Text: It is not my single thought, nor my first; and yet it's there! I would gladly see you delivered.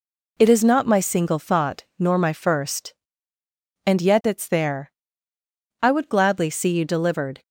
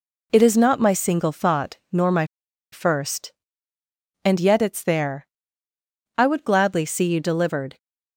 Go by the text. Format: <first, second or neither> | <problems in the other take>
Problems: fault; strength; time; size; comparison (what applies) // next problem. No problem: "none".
first | pauses between "my" and "first"; noticeable; at 2.2 s; 0.48 s long